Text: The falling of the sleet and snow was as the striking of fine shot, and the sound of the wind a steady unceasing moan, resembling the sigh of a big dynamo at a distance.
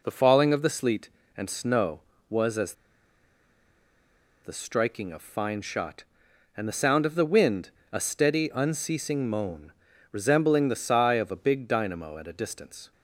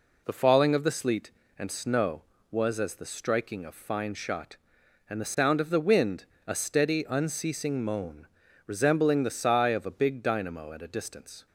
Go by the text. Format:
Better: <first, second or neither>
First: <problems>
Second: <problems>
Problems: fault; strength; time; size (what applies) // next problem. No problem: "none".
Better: second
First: pauses between "as" and "the"; strong; at 2.7 s; 1.7 s long // pauses between "wind" and "a"; slight; at 7.6 s; 0.24 s long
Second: pauses between "wind" and "a"; slight; at 6.2 s; 0.24 s long